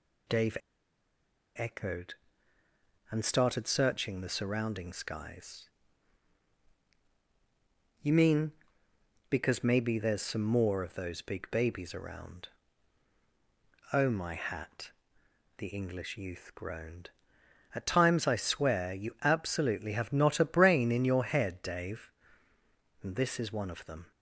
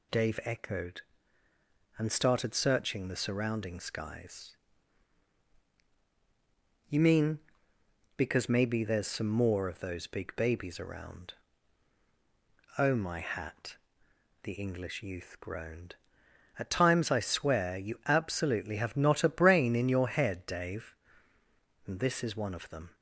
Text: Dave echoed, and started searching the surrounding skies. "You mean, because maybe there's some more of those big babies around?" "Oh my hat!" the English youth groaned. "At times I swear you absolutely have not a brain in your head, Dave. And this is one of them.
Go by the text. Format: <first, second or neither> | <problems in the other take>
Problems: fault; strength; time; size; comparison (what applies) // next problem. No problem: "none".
second | pauses between "Dave" and "echoed"; at 0.5 s; 0.99 s long